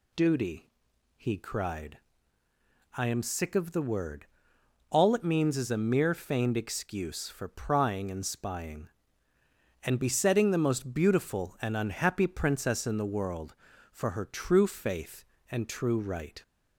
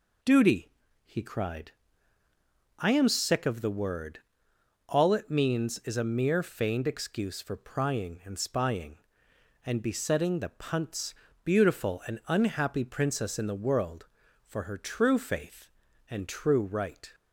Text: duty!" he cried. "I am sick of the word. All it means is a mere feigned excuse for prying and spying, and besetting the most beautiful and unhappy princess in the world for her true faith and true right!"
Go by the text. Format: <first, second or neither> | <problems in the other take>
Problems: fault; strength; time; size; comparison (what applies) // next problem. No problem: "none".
first | says "punts" for "most"; at 10.4 s